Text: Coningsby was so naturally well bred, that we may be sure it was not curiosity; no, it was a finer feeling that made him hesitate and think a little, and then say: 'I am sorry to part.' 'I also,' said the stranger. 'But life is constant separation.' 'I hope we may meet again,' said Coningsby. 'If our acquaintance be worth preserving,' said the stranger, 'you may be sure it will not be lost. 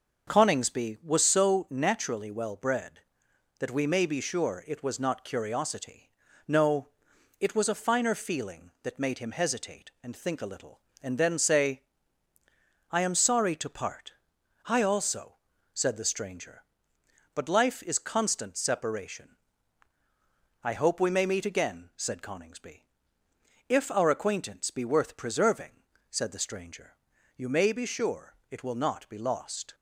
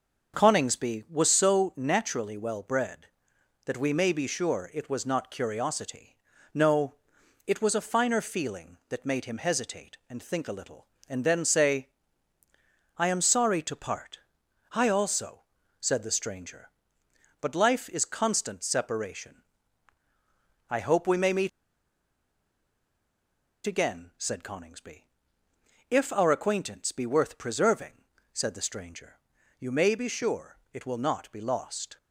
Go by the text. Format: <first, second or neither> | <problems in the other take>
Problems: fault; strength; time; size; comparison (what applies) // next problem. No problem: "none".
first | starts louder than the rest; until 1.3 s; 6.5 dB; also in the first // pauses between "meet" and "again"; strong; at 21.4 s; 2.1 s long // pauses between "sure" and "it"; slight; at 30.5 s; 0.16 s long; slight in the first